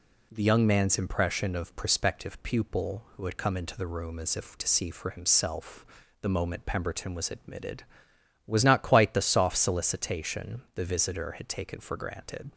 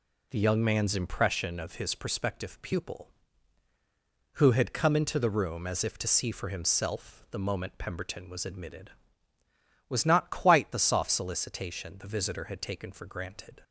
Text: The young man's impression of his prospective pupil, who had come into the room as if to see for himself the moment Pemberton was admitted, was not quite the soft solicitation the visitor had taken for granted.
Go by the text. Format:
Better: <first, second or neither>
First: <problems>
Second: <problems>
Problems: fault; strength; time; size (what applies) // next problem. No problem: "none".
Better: second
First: skips "his"; at 1.7 s // pauses between "himself" and "the"; slight; at 5.8 s; 0.36 s long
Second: none